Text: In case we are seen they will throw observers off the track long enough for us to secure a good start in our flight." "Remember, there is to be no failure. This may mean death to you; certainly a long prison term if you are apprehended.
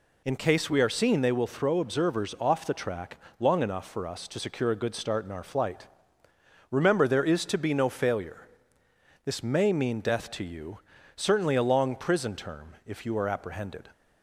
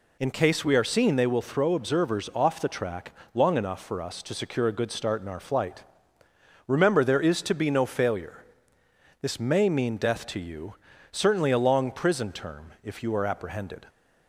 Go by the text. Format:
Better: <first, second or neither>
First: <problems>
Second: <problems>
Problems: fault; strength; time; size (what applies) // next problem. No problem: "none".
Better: neither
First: pauses between "track" and "long"; slight; at 3.1 s; 0.22 s long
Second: pauses between "track" and "long"; slight; at 3.1 s; 0.22 s long